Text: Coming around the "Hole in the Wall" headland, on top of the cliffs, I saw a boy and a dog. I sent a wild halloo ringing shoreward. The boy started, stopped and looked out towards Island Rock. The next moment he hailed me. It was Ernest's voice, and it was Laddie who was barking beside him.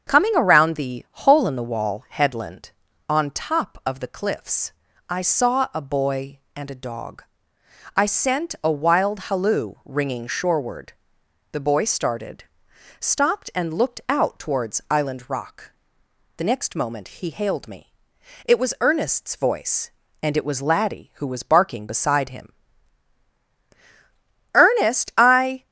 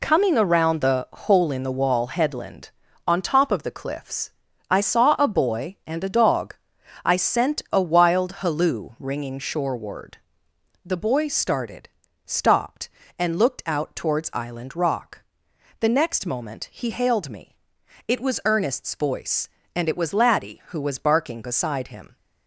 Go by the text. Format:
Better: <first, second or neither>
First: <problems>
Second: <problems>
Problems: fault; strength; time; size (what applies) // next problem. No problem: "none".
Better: second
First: starts louder than the rest; until 1.1 s; 7 dB // goes on to say "Ernest I"; noticeable; from 24.5 s on; 1.1 s long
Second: none